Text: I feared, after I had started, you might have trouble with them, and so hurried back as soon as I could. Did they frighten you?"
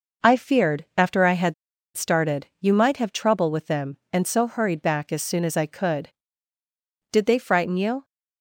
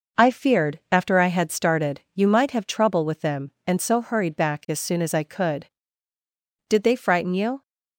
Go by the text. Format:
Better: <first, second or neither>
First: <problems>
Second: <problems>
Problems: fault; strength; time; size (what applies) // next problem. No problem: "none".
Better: second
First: pauses between "had" and "started"; at 1.5 s; 0.42 s long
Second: none